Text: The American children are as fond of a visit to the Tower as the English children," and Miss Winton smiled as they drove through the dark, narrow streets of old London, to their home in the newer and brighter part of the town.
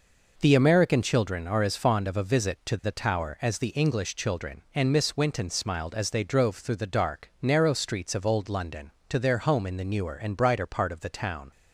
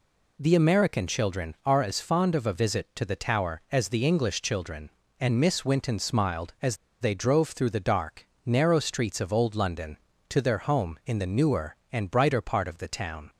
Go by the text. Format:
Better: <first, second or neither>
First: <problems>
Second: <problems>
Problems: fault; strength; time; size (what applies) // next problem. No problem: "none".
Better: first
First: none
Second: pauses between "as" and "they"; slight; at 6.7 s; 0.24 s long